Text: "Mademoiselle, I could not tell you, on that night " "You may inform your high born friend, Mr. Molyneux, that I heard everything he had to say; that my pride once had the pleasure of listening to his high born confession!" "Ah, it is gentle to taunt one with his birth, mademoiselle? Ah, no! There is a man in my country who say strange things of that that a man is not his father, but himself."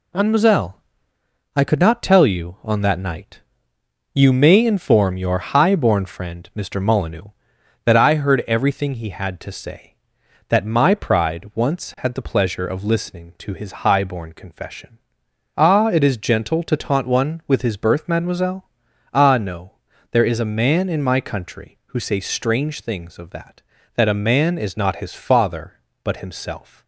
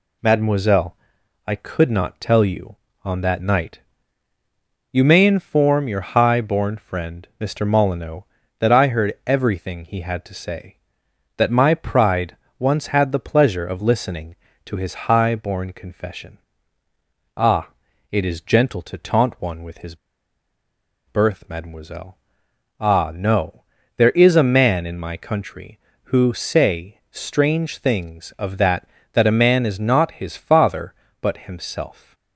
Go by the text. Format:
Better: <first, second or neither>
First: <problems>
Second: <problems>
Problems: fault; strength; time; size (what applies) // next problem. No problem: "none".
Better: first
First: none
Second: pauses between "pride" and "once"; slight; at 12.3 s; 0.24 s long // pauses between "his" and "birth"; at 19.9 s; 1.1 s long